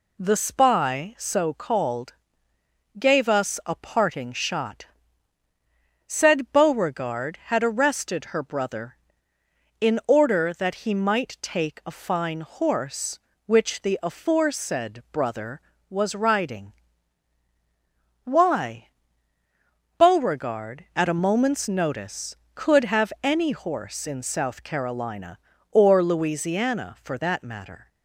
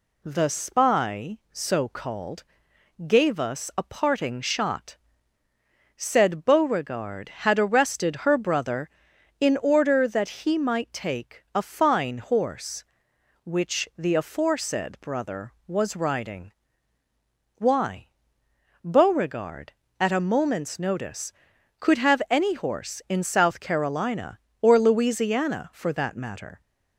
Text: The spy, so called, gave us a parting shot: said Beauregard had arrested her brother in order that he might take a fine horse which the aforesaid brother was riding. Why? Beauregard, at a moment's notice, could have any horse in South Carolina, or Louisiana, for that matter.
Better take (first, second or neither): neither